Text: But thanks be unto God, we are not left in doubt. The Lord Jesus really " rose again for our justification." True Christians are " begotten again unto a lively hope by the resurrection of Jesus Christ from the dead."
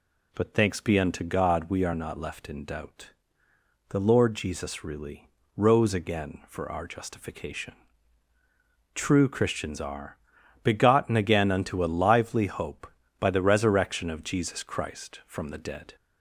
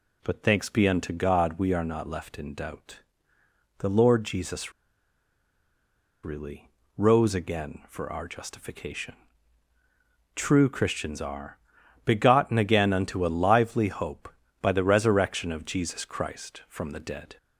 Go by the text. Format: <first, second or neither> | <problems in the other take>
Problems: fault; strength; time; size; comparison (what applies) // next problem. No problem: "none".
first | pauses between "Jesus" and "really"; strong; at 4.7 s; 1.5 s long